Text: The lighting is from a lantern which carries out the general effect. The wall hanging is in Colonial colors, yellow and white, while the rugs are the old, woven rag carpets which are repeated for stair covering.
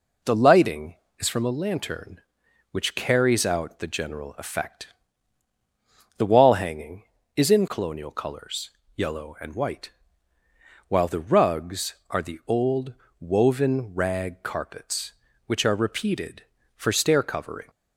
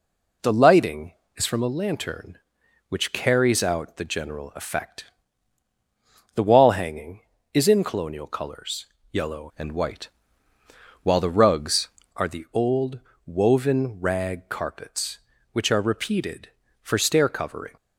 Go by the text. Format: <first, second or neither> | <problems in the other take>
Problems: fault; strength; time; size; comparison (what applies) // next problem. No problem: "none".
first | changes voice from "and" to "rugs"; from 9.5 to 11.8 s; 2.3 s long